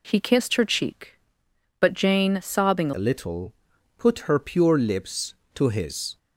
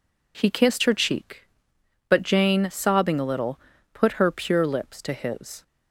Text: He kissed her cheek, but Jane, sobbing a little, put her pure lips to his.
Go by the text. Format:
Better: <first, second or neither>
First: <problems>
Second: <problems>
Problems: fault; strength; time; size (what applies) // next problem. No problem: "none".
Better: second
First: changes voice at "a"; from 2.9 s on; 3.2 s long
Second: none